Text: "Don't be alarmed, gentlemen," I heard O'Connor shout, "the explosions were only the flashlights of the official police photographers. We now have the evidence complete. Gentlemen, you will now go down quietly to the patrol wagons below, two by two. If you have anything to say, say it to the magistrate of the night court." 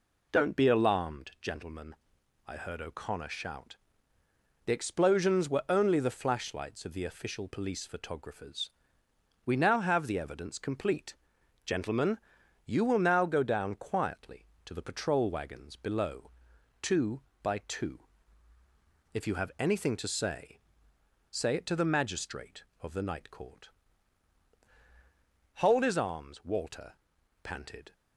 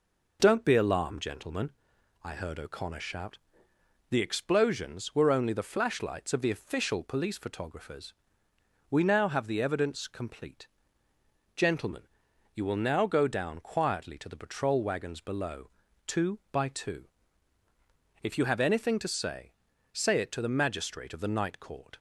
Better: second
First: goes on to say "Hold his arms Walter panted"; strong; from 25.5 s on; 2.3 s long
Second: none

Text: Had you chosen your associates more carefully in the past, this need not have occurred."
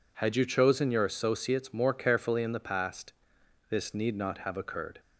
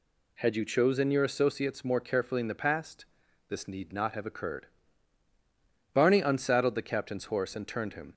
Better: first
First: none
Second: goes on to say "Barney unsaddled the captain's horse and turned him"; strong; from 5.9 s on; 2.1 s long

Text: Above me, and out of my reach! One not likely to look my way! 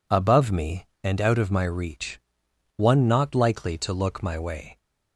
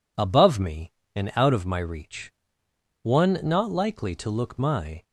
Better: first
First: none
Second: stops before "way"; at 5.0 s

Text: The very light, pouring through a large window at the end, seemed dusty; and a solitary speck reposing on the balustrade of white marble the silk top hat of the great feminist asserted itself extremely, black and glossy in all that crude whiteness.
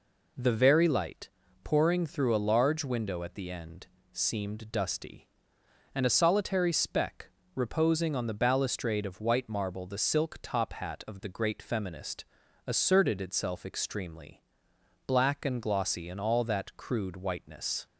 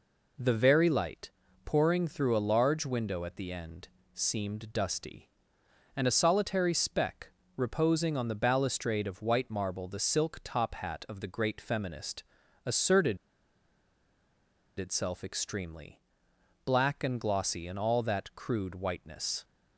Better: first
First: pauses between "speck" and "reposing"; slight; at 7.3 s; 0.26 s long // pauses between "feminist" and "asserted"; at 12.2 s; 0.40 s long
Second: pauses between "speck" and "reposing"; slight; at 7.3 s; 0.26 s long // pauses between "feminist" and "asserted"; at 12.2 s; 0.40 s long // pauses between "asserted" and "itself"; strong; at 13.1 s; 1.6 s long

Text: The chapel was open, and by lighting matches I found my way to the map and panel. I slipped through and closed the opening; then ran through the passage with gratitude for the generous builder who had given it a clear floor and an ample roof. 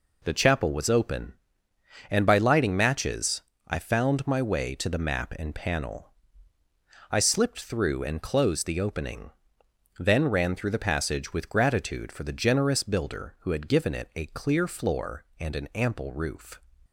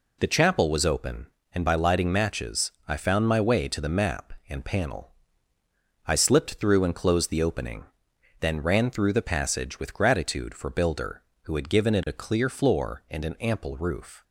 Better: first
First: pauses between "matches" and "I"; slight; at 3.4 s; 0.26 s long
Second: pauses between "matches" and "I"; slight; at 2.7 s; 0.16 s long // skips "the generous"; at 10.7 s

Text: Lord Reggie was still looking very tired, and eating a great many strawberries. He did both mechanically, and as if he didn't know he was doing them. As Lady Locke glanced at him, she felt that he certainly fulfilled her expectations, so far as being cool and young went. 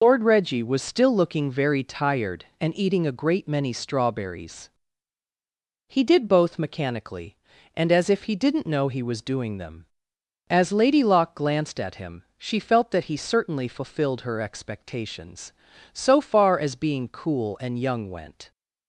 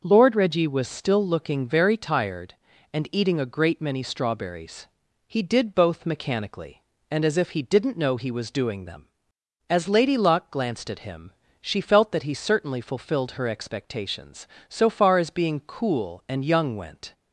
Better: second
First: loses the start of "Lord"; at 0.0 s; 70 ms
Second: none

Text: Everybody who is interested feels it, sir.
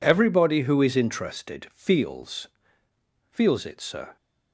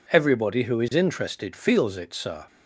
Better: second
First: says "feels" twice; at 3.2 s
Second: none

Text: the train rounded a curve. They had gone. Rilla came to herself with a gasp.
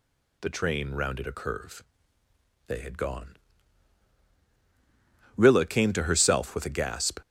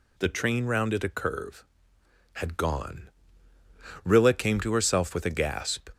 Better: first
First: none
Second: skips "They"; at 1.9 s

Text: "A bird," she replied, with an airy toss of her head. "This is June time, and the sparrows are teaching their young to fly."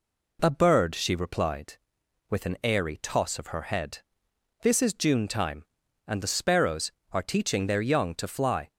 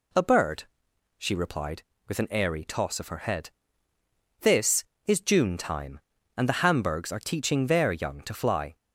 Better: first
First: none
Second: says "hamburgs" for "sparrows"; at 6.6 s

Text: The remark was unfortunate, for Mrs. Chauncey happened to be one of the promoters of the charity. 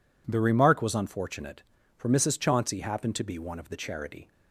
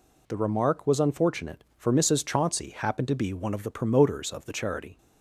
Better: second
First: skips "the promoters of"; at 3.6 s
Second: none

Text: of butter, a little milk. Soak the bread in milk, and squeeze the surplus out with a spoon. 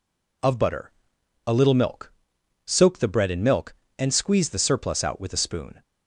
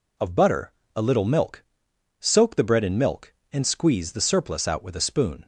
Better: neither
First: none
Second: none

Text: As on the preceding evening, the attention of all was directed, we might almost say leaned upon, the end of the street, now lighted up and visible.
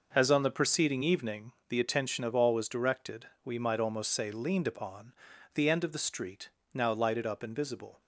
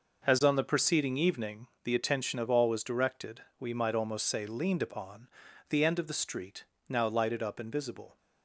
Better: neither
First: none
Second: none

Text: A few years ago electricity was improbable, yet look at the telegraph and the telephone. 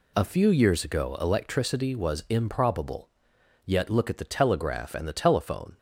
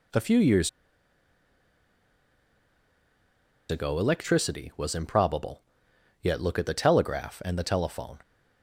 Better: first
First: none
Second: pauses between "years" and "ago"; strong; at 0.6 s; 3.0 s long

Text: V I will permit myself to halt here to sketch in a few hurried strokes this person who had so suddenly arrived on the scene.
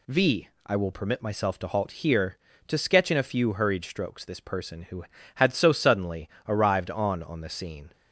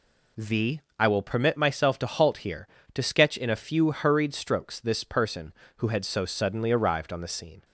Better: second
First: pauses between "V" and "I"; slight; at 0.4 s; 0.18 s long // pauses between "suddenly" and "arrived"; slight; at 6.2 s; 0.18 s long // says "on" twice; at 7.2 s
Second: pauses between "V" and "I"; slight; at 0.8 s; 0.16 s long

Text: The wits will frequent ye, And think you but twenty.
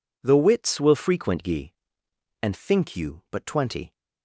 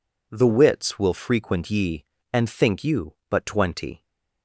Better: neither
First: none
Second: none

